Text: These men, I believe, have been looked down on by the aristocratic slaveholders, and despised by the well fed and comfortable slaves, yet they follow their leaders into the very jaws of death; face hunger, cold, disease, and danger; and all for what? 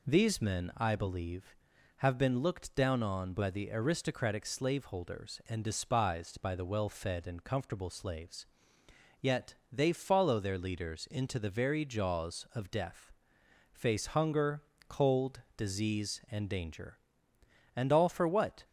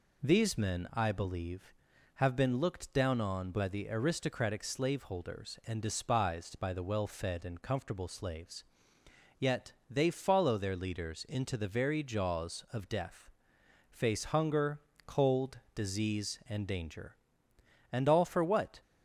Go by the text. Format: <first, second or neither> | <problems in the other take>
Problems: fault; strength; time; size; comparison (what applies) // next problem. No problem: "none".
neither | pauses between "yet" and "they"; slight; the same in both